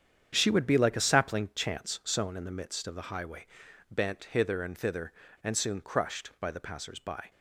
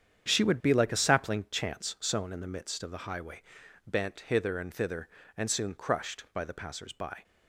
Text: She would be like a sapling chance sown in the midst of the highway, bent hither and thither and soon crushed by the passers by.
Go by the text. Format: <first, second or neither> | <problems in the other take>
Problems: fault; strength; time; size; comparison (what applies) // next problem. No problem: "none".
neither | starts louder than the rest; strong; the same in both